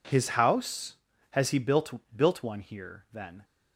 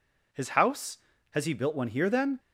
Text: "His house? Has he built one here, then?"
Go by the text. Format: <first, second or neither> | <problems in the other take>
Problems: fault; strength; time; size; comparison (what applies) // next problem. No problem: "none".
second | says "built" twice; at 2.1 s